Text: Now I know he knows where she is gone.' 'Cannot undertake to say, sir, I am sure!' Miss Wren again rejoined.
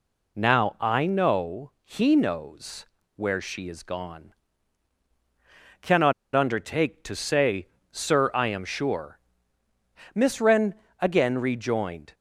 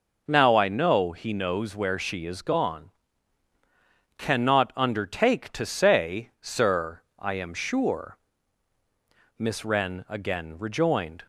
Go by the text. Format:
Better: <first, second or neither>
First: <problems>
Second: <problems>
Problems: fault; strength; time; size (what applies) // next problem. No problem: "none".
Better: second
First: pauses between "knows" and "where"; slight; at 2.8 s; 0.30 s long // pauses between "Cannot" and "undertake"; slight; at 6.1 s; 0.22 s long // pauses between "Wren" and "again"; slight; at 10.7 s; 0.24 s long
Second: none